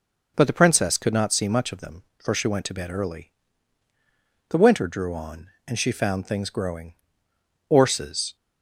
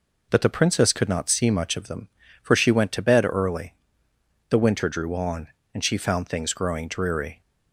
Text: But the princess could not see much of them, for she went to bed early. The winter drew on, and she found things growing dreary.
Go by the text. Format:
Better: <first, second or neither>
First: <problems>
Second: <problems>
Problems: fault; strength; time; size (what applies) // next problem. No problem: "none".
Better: second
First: says "orses" for "dreary"; at 7.6 s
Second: none